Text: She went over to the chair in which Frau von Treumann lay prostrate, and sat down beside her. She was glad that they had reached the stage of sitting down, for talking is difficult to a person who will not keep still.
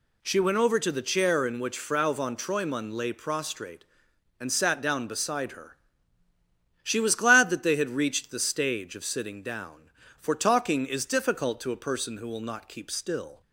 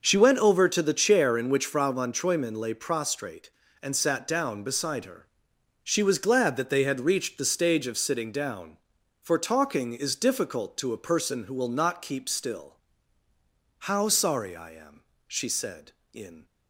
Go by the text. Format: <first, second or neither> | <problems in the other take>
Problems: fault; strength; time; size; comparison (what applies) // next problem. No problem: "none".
first | goes on to say "How sorry I am she said in"; strong; from 13.8 s on; 2.5 s long